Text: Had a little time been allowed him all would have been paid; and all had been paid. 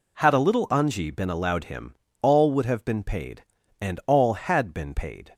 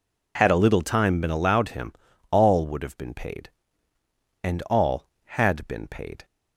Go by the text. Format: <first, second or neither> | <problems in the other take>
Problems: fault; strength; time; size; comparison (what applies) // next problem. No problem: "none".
second | says "anji" for "time"; at 0.6 s // pauses between "him" and "all"; slight; at 1.9 s; 0.26 s long; slight in the second